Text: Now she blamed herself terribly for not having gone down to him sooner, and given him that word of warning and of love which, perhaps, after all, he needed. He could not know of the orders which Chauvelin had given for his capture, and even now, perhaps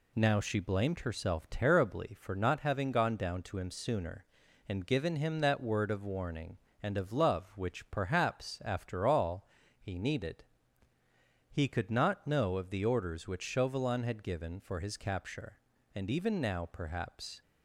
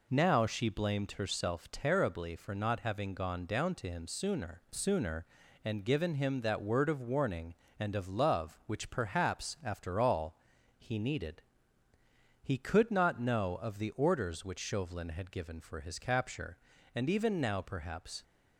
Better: first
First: none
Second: says "sooner" twice; at 4.7 s

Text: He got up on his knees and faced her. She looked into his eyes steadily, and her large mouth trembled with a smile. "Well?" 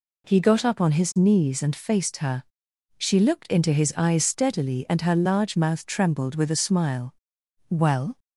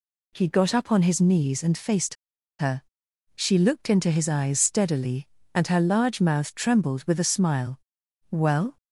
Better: first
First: none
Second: pauses between "faced" and "her"; at 2.1 s; 0.44 s long

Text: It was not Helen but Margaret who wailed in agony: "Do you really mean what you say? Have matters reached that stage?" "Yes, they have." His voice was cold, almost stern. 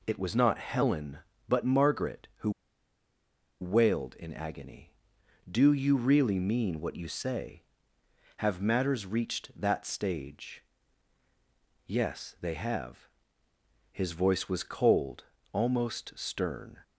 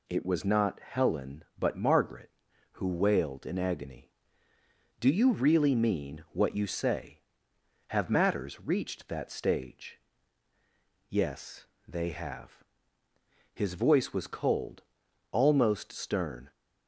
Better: second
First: pauses between "who" and "wailed"; at 2.5 s; 1.1 s long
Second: none

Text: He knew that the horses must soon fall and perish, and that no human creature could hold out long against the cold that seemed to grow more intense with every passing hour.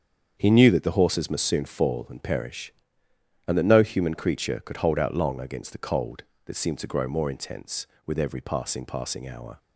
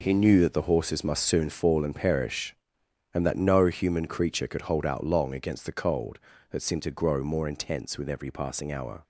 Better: second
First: starts louder than the rest; strong; until 1.3 s; 7.5 dB // says "passing" twice; at 8.8 s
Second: none

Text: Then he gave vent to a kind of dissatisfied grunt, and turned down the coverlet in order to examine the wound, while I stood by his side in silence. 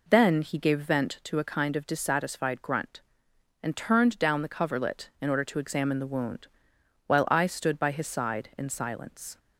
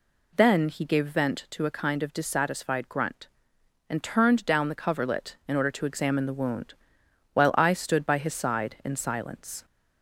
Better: second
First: gets quieter; throughout; 3.5 dB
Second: none

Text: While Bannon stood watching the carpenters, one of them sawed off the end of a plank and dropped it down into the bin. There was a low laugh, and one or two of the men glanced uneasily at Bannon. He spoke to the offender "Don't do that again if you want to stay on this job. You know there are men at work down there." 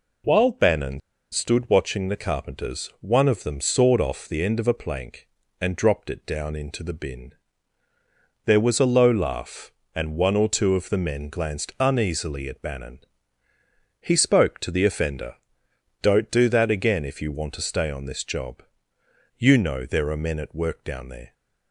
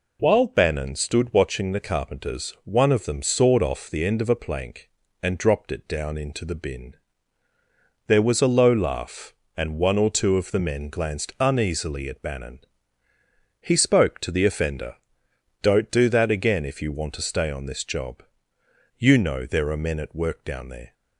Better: second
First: pauses between "Bannon" and "stood"; slight; at 1.0 s; 0.32 s long // pauses between "offender" and "Don't"; noticeable; at 15.3 s; 0.66 s long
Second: pauses between "offender" and "Don't"; noticeable; at 14.9 s; 0.66 s long

